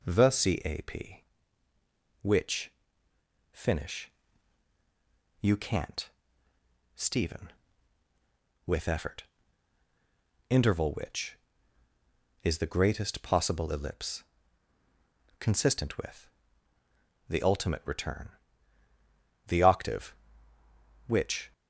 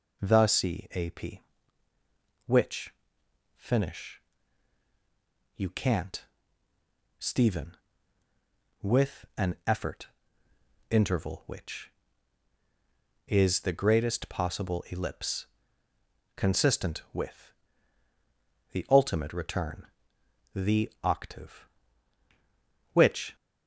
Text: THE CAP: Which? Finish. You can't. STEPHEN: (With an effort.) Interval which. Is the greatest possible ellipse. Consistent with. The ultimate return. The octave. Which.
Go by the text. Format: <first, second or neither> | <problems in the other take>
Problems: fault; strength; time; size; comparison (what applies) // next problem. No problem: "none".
second | skips "an"; at 8.8 s